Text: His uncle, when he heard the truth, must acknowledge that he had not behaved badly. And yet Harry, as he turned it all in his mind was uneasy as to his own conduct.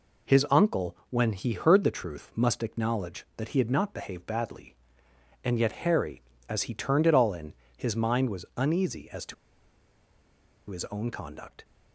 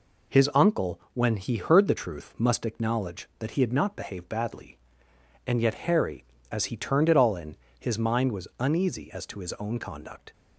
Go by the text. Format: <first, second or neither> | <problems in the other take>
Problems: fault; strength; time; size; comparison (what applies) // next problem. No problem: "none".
second | pauses between "in" and "his"; slight; at 7.5 s; 0.24 s long; slight in the second // pauses between "to" and "his"; strong; at 9.3 s; 1.3 s long